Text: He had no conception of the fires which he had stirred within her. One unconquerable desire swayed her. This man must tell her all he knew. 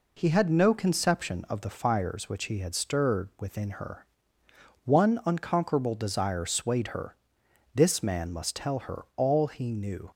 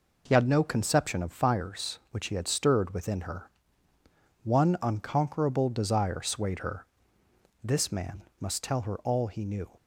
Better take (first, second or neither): first